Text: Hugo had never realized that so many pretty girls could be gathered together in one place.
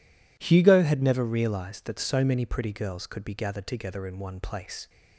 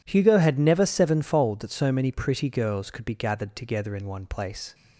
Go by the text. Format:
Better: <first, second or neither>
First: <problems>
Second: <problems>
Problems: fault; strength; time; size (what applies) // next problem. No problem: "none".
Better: first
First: none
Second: says "sevenfold" for "realized"; at 0.8 s